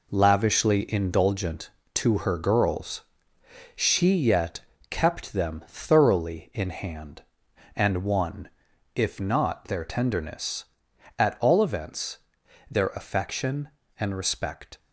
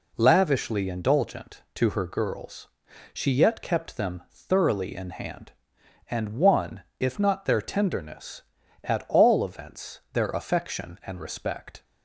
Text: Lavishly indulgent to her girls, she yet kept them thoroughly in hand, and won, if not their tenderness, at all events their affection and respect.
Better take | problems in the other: second | gets quieter; strong; throughout; 7.5 dB // pauses between "yet" and "kept"; slight; at 4.6 s; 0.28 s long // pauses between "events" and "their"; noticeable; at 12.1 s; 0.52 s long

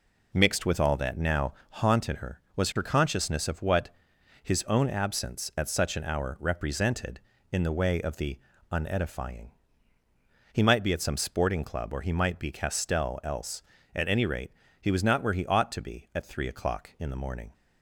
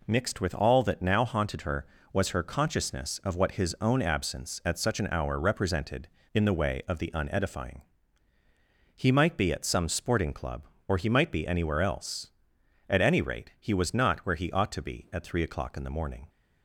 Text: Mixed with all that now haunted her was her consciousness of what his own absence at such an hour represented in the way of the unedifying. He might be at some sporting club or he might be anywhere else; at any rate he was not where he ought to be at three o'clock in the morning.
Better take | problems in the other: second | pauses between "now" and "haunted"; slight; at 1.5 s; 0.18 s long // pauses between "what" and "his"; noticeable; at 3.8 s; 0.54 s long // pauses between "the" and "unedifying"; slight; at 8.3 s; 0.34 s long // says "castell" for "anywhere"; at 12.5 s // pauses between "rate" and "he"; slight; at 14.5 s; 0.30 s long

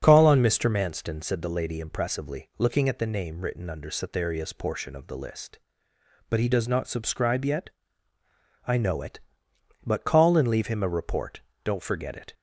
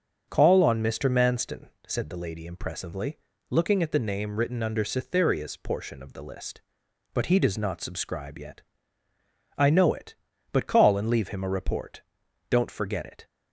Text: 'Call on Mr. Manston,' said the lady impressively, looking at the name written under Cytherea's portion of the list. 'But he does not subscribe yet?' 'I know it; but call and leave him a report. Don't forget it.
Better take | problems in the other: neither | starts louder than the rest; the same in both

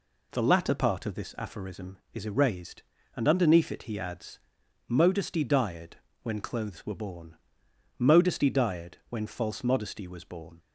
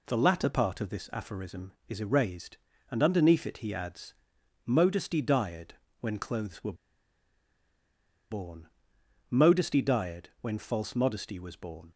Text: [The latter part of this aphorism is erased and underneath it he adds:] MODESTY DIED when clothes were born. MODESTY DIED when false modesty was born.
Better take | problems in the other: first | pauses between "DIED" and "when"; slight; at 5.7 s; 0.26 s long; slight in the first // pauses between "were" and "born"; strong; at 6.7 s; 1.5 s long

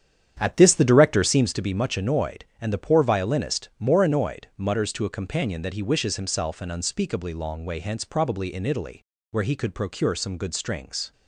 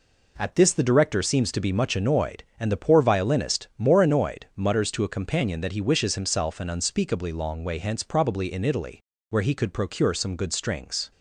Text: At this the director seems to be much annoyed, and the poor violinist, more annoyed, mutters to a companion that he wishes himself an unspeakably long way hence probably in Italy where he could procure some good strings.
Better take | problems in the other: second | starts louder than the rest; strong; until 1.6 s; 9 dB // pauses between "Italy" and "where"; slight; at 9.0 s; 0.28 s long; slight in the second

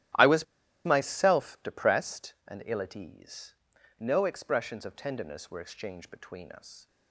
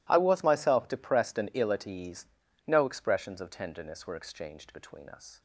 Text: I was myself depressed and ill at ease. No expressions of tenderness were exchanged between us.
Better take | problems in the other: second | starts louder than the rest; strong; until 1.5 s; 14.5 dB // pauses between "was" and "myself"; at 0.4 s; 0.40 s long

